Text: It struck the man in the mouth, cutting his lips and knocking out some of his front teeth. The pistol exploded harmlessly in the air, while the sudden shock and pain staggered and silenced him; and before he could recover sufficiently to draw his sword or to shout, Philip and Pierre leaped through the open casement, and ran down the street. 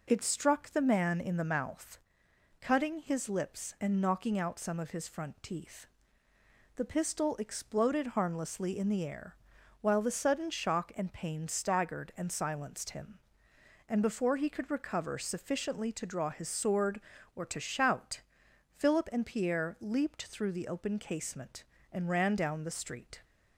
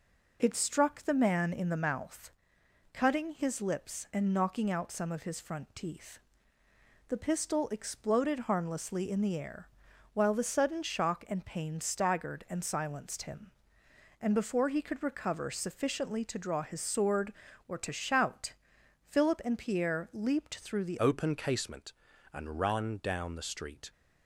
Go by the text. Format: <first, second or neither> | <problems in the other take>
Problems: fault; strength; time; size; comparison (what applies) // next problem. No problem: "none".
first | changes voice at "open"; from 21.0 s on; 2.9 s long